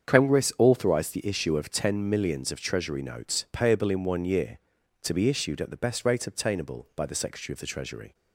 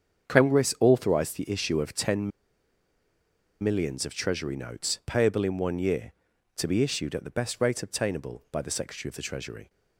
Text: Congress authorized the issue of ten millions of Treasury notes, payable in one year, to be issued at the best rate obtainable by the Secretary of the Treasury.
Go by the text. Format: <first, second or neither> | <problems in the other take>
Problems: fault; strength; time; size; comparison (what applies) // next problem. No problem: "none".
first | starts louder than the rest; strong; until 1.3 s; 7.5 dB; strong in the first // pauses between "ten" and "millions"; strong; at 2.3 s; 1.3 s long